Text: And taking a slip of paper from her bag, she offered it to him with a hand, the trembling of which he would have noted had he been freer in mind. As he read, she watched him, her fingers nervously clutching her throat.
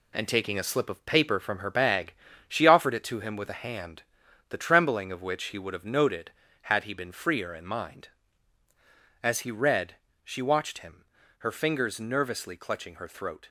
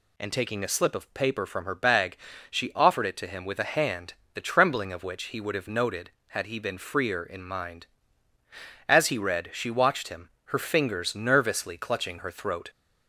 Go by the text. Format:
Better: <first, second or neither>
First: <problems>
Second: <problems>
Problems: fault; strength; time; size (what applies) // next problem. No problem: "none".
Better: second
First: gets quieter; throughout; 6.5 dB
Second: none